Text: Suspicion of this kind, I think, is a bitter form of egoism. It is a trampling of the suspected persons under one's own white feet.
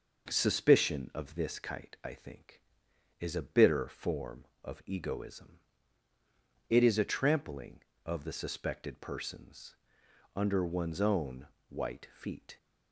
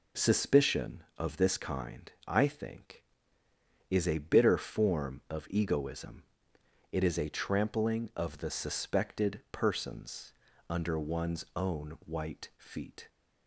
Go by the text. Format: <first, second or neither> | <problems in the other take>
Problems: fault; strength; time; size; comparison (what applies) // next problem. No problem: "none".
second | says "kite" for "kind"; at 1.5 s // pauses between "persons" and "under"; noticeable; at 9.7 s; 0.60 s long; also in the second // pauses between "own" and "white"; slight; at 11.4 s; 0.22 s long